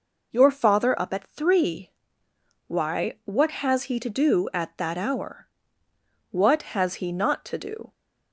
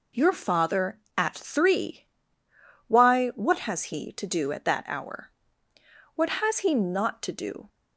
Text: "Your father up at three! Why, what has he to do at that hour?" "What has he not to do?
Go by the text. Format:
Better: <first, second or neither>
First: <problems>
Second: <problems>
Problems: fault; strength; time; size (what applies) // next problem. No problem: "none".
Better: first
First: none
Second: skips "up"; at 1.0 s